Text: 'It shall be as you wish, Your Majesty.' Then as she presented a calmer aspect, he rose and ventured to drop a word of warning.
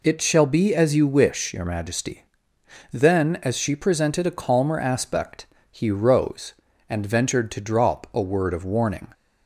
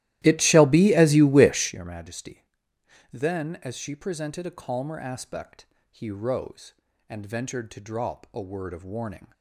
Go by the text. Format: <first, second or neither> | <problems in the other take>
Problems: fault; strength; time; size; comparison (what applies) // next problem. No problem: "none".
first | starts louder than the rest; strong; until 1.8 s; 15 dB